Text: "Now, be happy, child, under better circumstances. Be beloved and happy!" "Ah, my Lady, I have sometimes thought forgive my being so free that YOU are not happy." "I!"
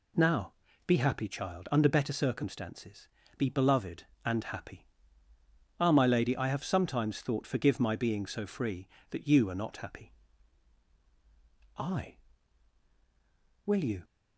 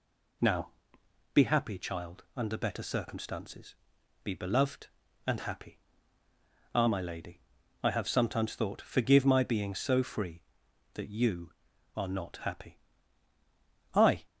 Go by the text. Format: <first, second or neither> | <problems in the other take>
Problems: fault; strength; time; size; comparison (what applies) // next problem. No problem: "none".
second | goes on to say "Will you"; slight; from 13.6 s on; 0.38 s long